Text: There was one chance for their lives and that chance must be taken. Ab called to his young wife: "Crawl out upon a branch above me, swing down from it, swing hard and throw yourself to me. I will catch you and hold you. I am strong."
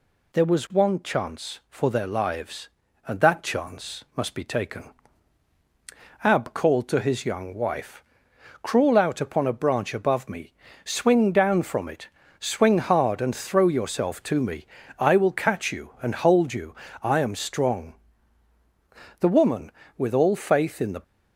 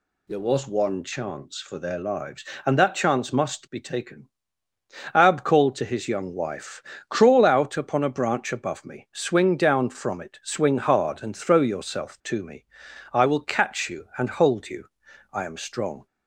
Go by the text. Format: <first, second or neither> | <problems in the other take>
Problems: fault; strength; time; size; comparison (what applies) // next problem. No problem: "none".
second | goes on to say "The woman with all faith in the"; strong; from 19.1 s on; 1.8 s long